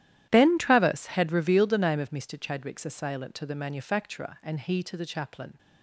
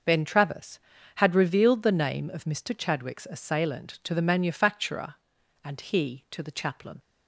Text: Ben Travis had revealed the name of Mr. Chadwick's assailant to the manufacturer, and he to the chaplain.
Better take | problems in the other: second | gets quieter; strong; throughout; 17 dB

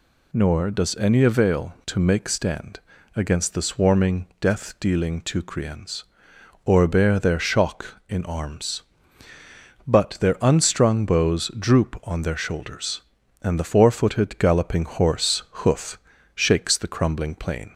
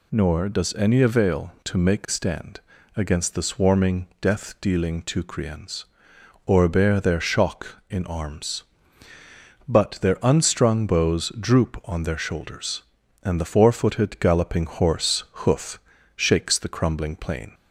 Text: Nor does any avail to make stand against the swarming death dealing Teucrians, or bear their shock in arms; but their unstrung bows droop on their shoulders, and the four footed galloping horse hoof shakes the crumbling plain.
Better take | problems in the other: neither | pauses between "stand" and "against"; slight; the same in both // pauses between "hoof" and "shakes"; slight; the same in both

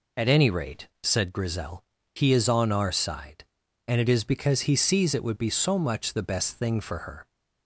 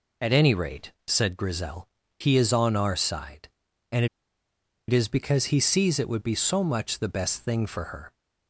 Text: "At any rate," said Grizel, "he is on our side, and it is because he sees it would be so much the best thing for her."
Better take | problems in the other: first | pauses between "and" and "it"; noticeable; at 4.0 s; 0.82 s long

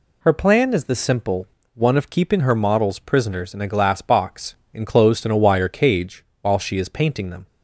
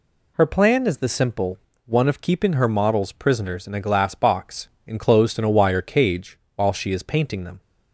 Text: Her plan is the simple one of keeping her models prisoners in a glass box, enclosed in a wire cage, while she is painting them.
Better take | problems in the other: neither | pauses between "simple" and "one"; slight; the same in both

